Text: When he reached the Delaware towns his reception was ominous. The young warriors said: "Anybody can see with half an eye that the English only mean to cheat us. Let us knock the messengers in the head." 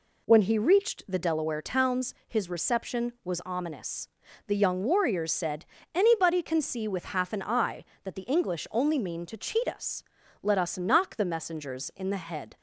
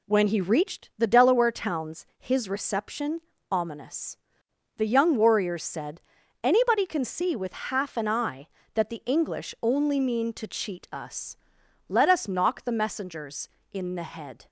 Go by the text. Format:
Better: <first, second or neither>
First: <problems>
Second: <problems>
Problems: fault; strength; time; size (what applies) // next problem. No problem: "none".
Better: first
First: none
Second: skips "was"; at 3.3 s